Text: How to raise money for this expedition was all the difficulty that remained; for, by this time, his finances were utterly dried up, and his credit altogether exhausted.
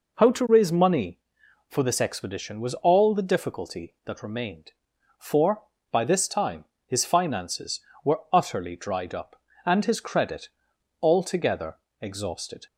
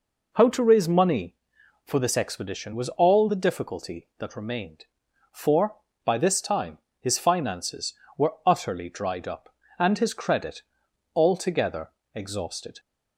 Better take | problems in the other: neither | pauses between "credit" and "altogether"; noticeable; the same in both // pauses between "altogether" and "exhausted"; slight; the same in both

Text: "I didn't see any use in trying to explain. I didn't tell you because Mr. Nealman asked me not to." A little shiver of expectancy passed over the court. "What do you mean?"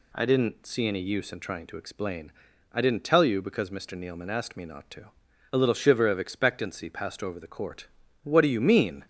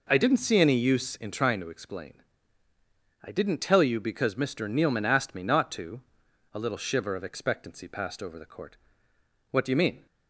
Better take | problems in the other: first | starts louder than the rest; noticeable; until 1.6 s; 4.5 dB

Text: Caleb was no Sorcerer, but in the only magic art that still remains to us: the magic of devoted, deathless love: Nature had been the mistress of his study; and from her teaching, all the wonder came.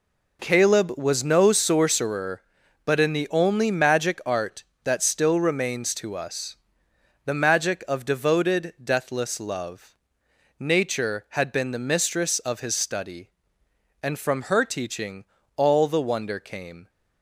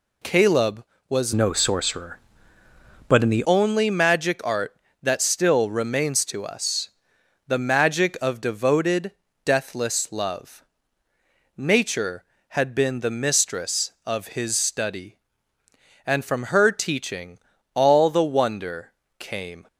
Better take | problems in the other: first | changes voice from "no" to "the"; from 1.3 to 3.4 s; 2.1 s long // pauses between "wonder" and "came"; slight; at 18.9 s; 0.26 s long

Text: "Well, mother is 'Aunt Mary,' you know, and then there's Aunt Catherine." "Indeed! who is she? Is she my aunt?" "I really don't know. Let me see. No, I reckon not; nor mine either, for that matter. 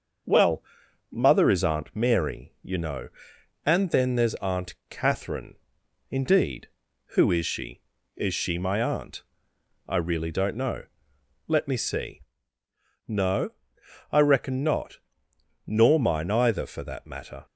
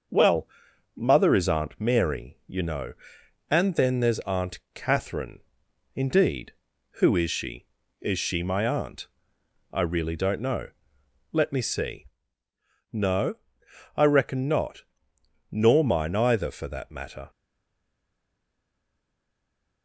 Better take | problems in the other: first | starts louder than the rest; until 1.5 s; 6.5 dB; also in the first // pauses between "Aunt" and "Catherine"; slight; at 4.5 s; 0.16 s long; slight in the first // stays silent after the last word; strong; from 17.2 s on; 2.6 s long

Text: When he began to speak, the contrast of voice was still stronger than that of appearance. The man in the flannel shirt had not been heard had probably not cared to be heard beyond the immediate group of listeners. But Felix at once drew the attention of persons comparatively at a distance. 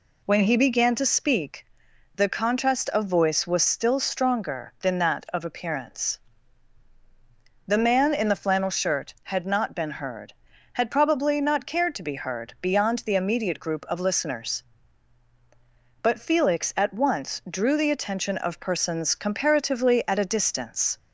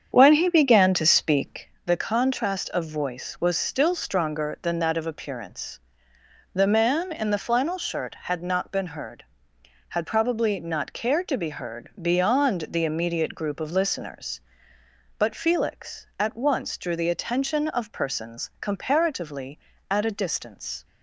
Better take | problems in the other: first | starts louder than the rest; strong; until 1.8 s; 7.5 dB

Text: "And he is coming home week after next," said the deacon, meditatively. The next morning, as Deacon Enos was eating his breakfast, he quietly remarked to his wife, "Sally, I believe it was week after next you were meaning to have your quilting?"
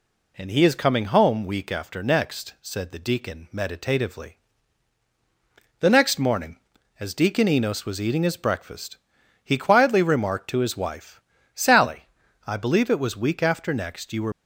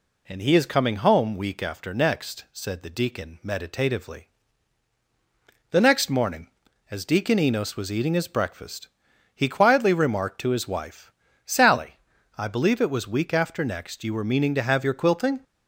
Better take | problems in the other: second | stops before "meaning to have your quilting"; at 14.3 s

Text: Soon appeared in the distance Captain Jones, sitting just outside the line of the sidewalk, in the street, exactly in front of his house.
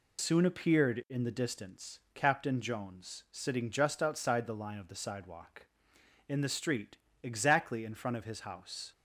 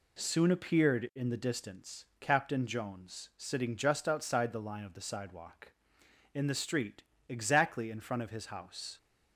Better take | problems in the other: second | loses the start of "Soon"; at 0.1 s; 80 ms // pauses between "distance" and "Captain"; slight; at 1.9 s; 0.16 s long; slight in the second

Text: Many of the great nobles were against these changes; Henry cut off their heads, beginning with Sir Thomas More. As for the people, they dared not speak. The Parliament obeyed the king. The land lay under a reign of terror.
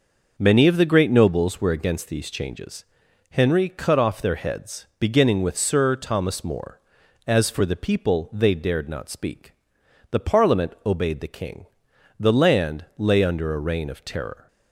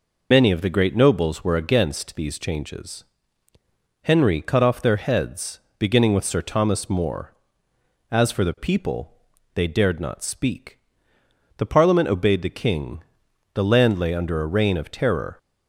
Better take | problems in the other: first | loses the start of "Many"; at 0.3 s; 60 ms

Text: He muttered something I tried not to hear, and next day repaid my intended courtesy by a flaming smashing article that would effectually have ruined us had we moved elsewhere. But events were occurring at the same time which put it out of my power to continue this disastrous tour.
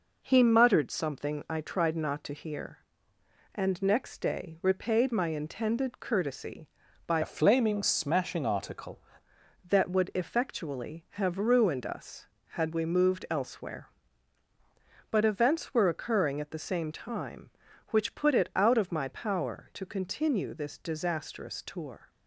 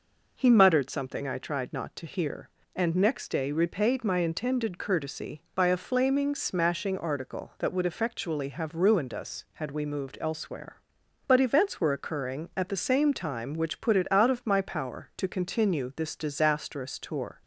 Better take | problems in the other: second | changes voice from "a" to "article"; from 7.2 to 8.9 s; 1.7 s long

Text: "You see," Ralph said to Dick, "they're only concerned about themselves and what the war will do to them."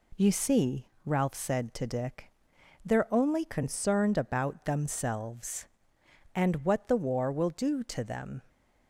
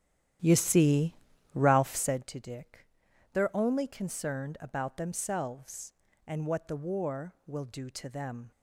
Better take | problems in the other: first | starts louder than the rest; strong; until 2.2 s; 11.5 dB

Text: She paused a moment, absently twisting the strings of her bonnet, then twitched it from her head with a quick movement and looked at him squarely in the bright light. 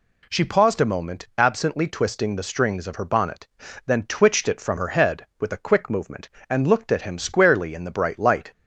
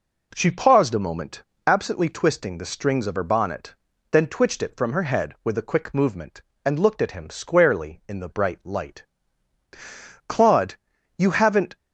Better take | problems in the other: first | goes on to say "Claude you haven't"; from 10.2 s on; 1.4 s long

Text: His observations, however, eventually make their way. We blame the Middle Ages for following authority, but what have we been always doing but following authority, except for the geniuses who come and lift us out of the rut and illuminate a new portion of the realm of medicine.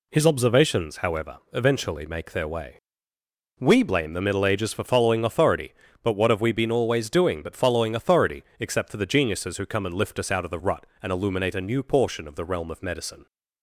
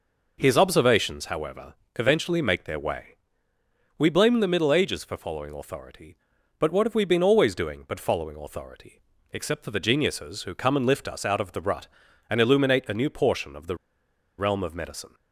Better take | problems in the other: first | pauses between "the" and "realm"; noticeable; at 13.7 s; 0.63 s long

